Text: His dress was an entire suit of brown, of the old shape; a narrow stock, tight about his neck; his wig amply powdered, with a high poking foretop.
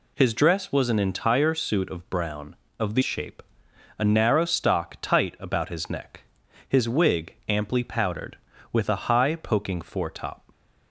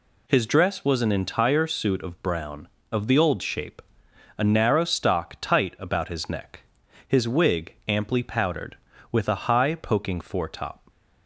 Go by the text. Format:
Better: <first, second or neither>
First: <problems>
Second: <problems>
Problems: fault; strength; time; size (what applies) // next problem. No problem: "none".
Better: second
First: skips "old"; at 3.0 s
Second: none